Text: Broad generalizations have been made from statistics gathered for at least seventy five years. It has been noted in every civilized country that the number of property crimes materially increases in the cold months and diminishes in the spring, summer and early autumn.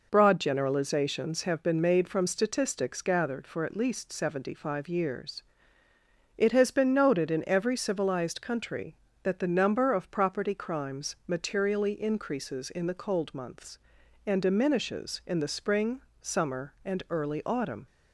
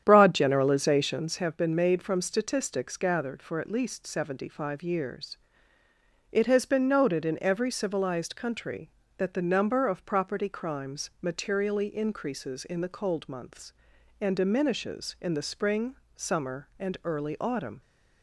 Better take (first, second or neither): first